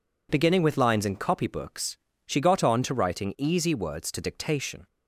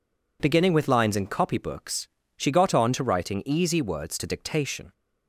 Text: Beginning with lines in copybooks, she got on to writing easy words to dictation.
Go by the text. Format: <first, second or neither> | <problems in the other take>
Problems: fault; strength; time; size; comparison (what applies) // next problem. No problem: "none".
neither | none